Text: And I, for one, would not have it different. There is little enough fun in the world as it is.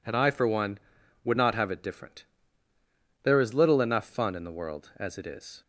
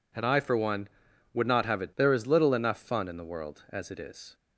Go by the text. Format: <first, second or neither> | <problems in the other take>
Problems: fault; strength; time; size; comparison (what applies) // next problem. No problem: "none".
first | skips "different"; at 1.9 s